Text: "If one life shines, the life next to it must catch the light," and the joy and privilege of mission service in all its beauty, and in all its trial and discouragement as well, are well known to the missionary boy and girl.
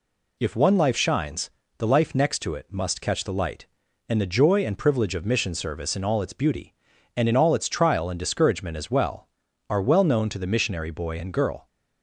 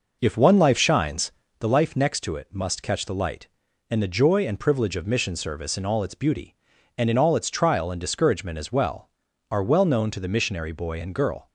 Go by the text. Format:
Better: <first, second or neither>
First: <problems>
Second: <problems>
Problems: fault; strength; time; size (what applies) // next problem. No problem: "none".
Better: first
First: none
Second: starts louder than the rest; noticeable; until 1.7 s; 5.5 dB